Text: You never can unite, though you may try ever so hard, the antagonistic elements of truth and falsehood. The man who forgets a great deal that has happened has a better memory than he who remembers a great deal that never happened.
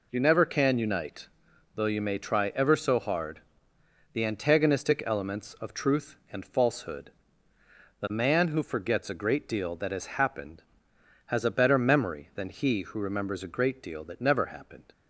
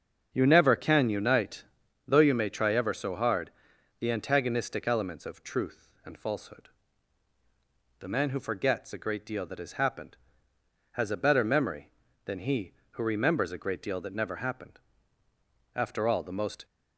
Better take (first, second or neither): first